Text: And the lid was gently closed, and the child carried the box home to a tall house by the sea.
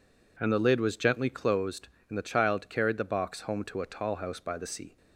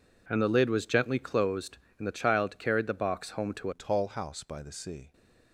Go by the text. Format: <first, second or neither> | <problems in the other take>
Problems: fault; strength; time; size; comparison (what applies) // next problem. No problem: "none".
first | changes voice at "a"; from 3.7 s on; 1.4 s long